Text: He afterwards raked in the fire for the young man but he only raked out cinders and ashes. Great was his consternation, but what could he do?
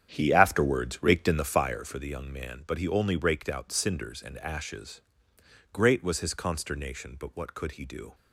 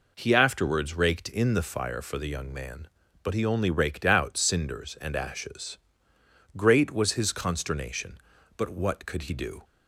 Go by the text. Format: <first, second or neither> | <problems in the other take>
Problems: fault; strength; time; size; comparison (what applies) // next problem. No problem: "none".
second | starts louder than the rest; strong; until 1.9 s; 9 dB